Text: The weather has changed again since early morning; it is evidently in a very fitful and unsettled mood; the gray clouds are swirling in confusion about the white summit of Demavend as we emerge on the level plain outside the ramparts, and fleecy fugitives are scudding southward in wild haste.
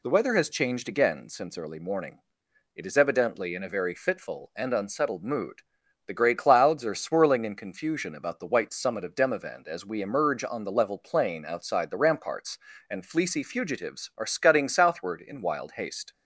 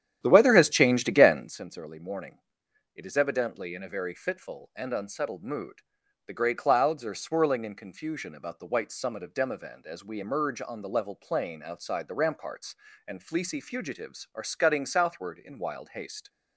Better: first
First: none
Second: starts louder than the rest; strong; until 1.6 s; 10.5 dB

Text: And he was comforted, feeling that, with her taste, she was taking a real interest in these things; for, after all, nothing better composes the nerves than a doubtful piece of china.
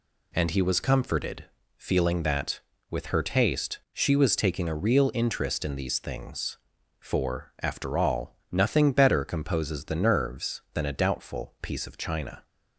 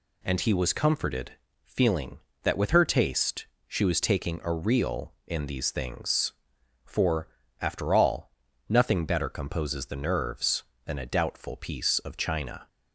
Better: first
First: none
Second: skips "interest"; at 5.1 s

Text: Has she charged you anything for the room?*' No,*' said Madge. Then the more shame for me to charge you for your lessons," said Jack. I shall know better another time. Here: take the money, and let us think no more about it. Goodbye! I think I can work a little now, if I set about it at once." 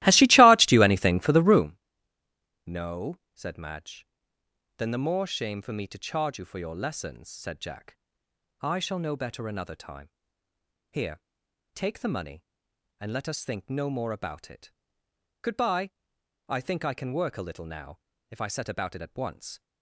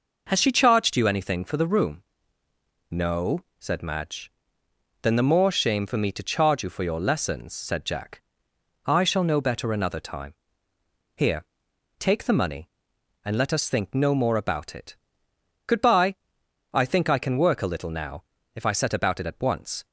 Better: second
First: starts louder than the rest; strong; until 1.8 s; 17 dB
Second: none

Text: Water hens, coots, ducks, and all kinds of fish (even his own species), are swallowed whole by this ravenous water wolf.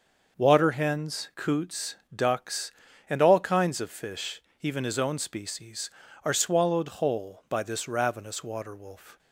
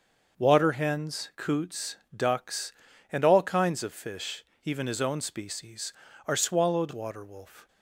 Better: first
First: starts louder than the rest; noticeable; until 1.4 s; 6 dB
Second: starts louder than the rest; noticeable; until 1.4 s; 6 dB // skips "whole by this ravenous"; at 6.9 s

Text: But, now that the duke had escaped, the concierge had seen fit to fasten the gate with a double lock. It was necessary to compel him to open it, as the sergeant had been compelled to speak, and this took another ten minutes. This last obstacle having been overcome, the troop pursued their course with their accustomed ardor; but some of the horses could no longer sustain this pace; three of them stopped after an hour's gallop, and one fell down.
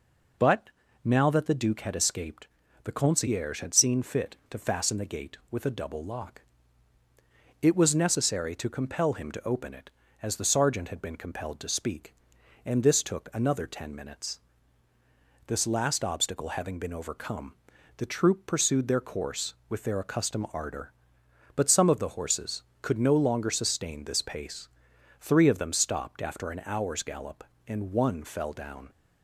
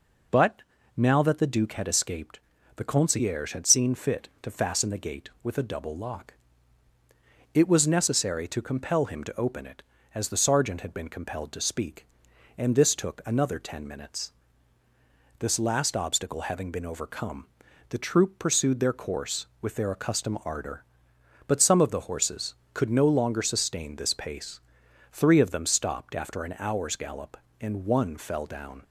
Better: neither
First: none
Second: none

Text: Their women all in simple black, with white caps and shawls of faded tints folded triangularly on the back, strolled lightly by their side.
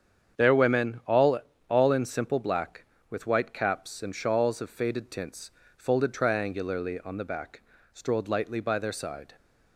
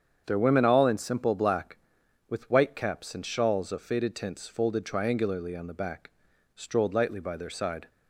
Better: second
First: starts louder than the rest; strong; until 1.7 s; 8 dB // says "all" twice; at 1.6 s // pauses between "tints" and "folded"; slight; at 5.5 s; 0.26 s long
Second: starts louder than the rest; strong; until 1.2 s; 7.5 dB

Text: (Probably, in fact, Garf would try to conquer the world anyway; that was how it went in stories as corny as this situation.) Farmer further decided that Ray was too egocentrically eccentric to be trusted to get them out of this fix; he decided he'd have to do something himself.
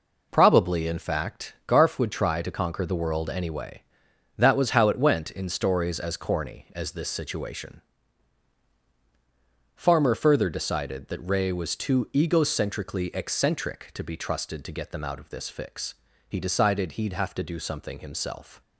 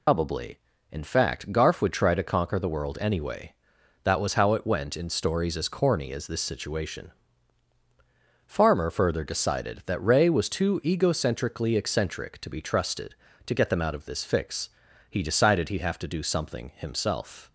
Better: first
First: none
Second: loses the start of "Probably"; at 0.0 s; 120 ms

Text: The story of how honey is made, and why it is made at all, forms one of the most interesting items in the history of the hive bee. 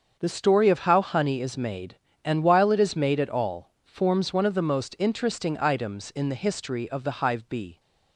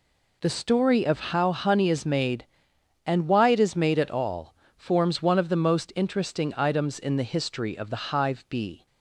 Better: second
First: starts louder than the rest; until 1.2 s; 7 dB // says "while" for "why"; at 2.4 s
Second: none

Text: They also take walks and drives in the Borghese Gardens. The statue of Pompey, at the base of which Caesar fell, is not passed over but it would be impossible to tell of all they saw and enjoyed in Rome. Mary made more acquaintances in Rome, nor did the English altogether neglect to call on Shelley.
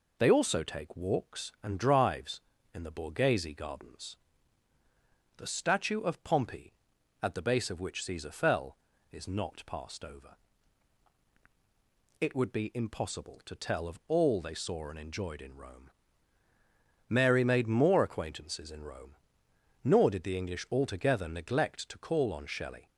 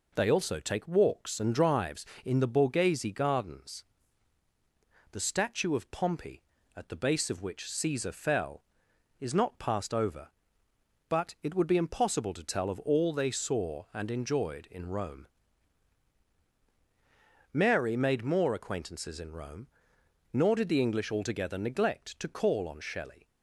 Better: second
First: skips "but"; at 11.2 s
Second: none

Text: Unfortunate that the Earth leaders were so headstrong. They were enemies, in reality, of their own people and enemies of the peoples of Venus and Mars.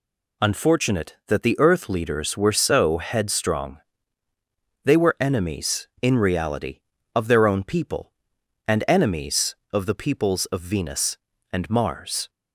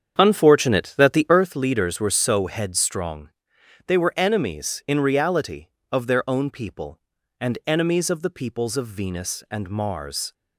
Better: first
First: none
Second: starts louder than the rest; strong; until 1.5 s; 8 dB

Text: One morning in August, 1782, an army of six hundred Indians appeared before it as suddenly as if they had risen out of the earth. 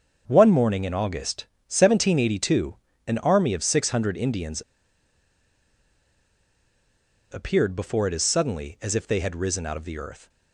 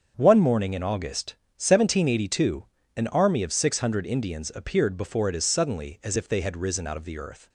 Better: second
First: starts louder than the rest; until 1.2 s; 7 dB // pauses between "Indians" and "appeared"; strong; at 4.6 s; 2.6 s long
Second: starts louder than the rest; strong; until 1.1 s; 7 dB

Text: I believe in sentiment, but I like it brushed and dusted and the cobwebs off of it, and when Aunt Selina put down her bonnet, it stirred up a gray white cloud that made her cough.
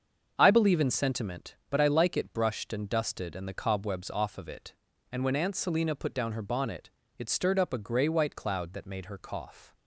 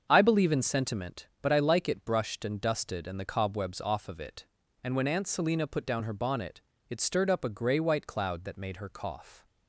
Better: neither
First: starts louder than the rest; until 1.3 s; 7 dB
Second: starts louder than the rest; until 1.1 s; 7 dB

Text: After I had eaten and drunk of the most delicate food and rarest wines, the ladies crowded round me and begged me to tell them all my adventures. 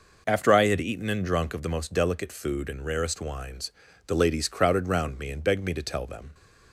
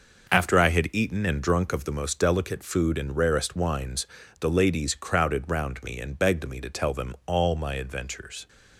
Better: second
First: stops before "all my adventures"; at 6.3 s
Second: none

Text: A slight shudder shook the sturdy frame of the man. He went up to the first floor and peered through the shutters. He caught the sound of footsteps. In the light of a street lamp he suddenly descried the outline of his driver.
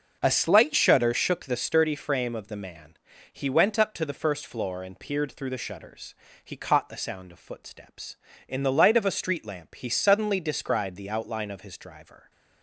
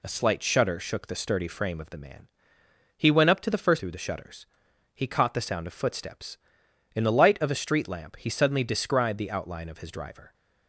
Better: first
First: none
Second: skips "floor and peered"; at 3.7 s

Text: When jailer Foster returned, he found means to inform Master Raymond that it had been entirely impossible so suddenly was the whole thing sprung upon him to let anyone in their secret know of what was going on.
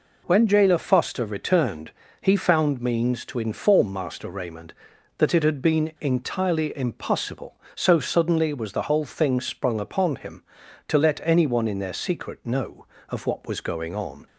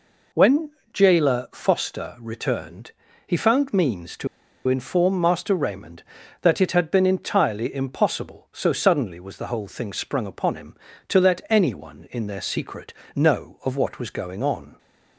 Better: first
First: none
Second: pauses between "When" and "jailer"; slight; at 0.6 s; 0.24 s long // pauses between "to" and "inform"; at 4.2 s; 0.40 s long // pauses between "secret" and "know"; slight; at 12.9 s; 0.24 s long

